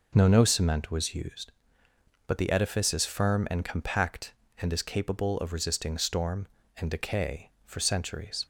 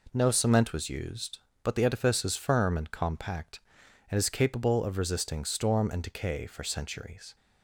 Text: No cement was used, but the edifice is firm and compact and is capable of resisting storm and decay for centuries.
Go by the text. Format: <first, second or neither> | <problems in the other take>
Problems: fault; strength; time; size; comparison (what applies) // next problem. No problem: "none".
second | says "No" twice; at 0.2 s